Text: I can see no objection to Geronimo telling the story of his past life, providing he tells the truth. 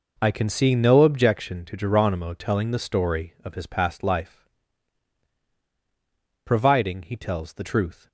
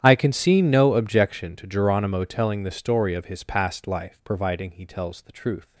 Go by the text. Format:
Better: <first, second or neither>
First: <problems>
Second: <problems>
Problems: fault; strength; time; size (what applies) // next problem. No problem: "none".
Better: first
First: none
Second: gets quieter; strong; throughout; 23 dB